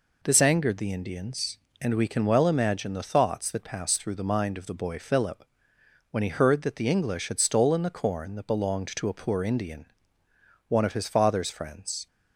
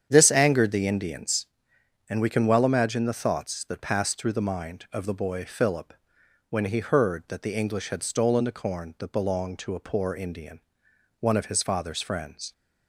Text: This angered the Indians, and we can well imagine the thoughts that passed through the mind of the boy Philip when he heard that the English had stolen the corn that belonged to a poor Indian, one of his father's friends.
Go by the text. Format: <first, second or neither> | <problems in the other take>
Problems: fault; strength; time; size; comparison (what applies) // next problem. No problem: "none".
first | starts louder than the rest; strong; until 1.6 s; 8.5 dB // pauses between "Philip" and "when"; noticeable; at 5.9 s; 0.56 s long; noticeable in the first